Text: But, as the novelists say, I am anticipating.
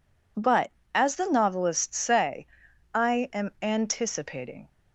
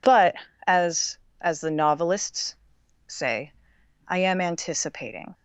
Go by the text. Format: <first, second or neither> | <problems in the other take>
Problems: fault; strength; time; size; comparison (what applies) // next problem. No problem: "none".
first | says "as" twice; at 1.3 s // pauses between "novelists" and "say"; noticeable; at 2.5 s; 0.52 s long